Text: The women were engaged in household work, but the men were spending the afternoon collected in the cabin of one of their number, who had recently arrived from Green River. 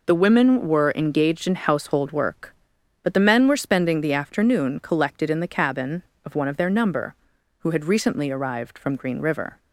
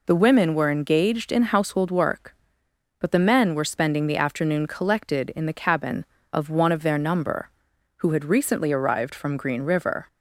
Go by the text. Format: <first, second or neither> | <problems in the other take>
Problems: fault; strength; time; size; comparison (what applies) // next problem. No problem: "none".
neither | none